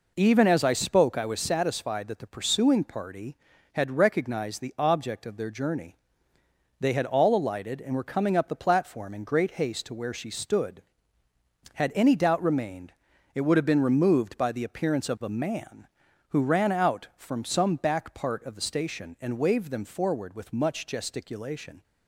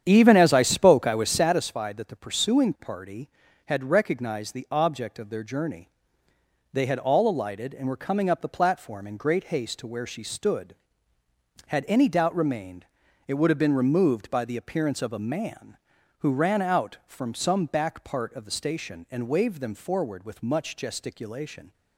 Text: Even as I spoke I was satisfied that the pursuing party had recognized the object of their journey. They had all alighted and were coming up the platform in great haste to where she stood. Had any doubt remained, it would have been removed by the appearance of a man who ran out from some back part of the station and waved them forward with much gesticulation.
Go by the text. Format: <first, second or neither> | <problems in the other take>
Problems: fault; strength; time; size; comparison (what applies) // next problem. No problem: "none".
first | starts louder than the rest; strong; until 1.7 s; 9 dB